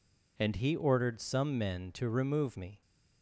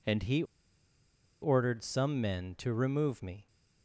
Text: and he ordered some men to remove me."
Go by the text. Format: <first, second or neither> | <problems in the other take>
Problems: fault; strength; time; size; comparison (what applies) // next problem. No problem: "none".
first | pauses between "he" and "ordered"; at 0.4 s; 0.98 s long